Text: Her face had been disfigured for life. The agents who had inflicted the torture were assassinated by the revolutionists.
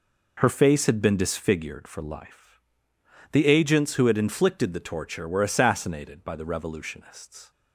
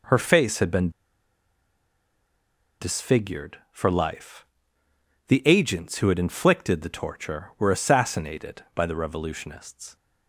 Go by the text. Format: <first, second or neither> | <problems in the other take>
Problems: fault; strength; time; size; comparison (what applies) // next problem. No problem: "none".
first | pauses between "been" and "disfigured"; strong; at 0.9 s; 1.8 s long